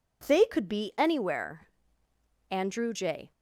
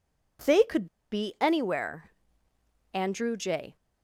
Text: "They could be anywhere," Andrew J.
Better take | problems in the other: first | pauses between "could" and "be"; slight; at 0.8 s; 0.25 s long

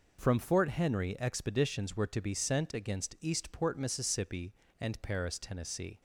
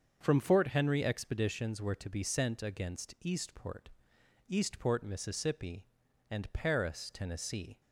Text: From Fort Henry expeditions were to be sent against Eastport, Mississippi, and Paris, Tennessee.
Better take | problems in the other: first | starts louder than the rest; until 1.2 s; 6.5 dB // says "Eastport" twice; at 4.5 s

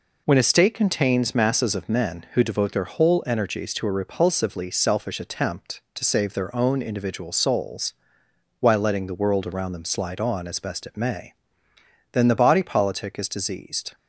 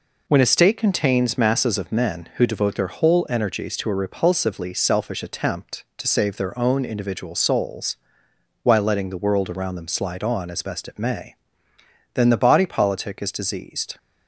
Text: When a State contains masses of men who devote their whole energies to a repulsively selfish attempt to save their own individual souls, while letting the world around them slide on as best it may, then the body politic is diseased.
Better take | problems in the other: neither | none

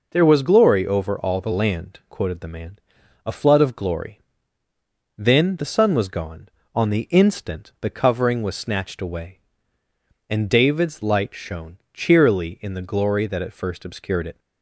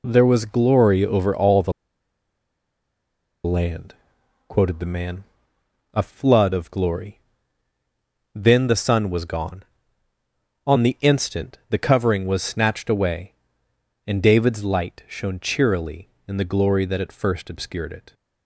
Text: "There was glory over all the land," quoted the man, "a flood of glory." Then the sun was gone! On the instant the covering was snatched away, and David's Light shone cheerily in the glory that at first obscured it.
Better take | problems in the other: first | pauses between "the" and "land"; strong; at 1.7 s; 1.7 s long

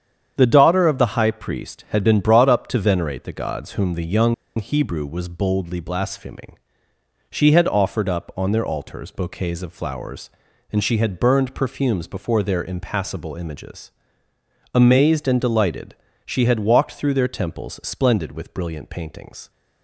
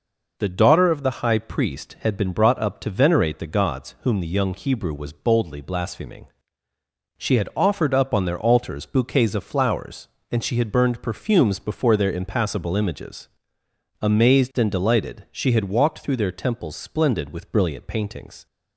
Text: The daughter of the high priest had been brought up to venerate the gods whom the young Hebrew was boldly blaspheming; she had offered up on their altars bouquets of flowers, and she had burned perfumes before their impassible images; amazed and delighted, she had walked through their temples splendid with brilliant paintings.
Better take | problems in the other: second | starts louder than the rest; strong; until 1.3 s; 8.5 dB // pauses between "young" and "Hebrew"; slight; at 4.3 s; 0.23 s long

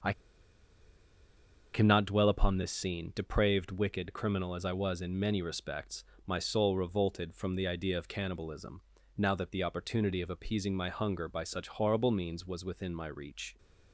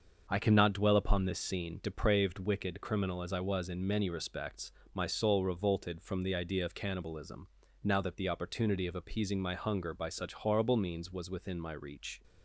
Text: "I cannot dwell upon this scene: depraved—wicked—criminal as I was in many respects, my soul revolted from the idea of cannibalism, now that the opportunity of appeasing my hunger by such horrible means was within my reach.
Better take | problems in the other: second | starts louder than the rest; until 2.6 s; 6.5 dB; also in the second // pauses between "I" and "cannot"; strong; at 0.1 s; 1.6 s long

